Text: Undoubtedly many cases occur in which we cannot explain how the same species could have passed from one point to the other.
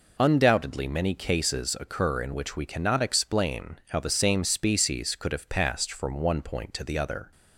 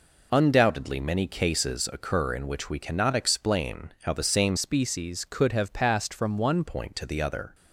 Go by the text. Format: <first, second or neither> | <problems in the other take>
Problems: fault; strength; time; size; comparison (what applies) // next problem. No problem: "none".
first | changes voice from "species" to "one"; from 4.5 to 6.6 s; 2.1 s long